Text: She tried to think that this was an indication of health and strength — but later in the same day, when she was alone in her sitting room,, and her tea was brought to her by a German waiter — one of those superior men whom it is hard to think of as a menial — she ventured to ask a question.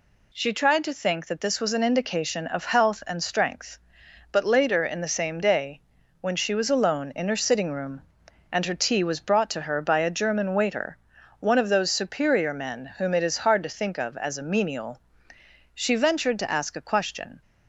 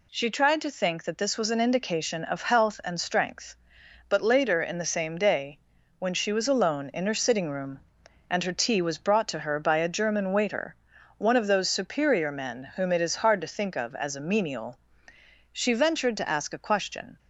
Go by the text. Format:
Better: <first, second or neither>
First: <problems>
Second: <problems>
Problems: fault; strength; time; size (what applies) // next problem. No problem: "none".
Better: neither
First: none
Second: none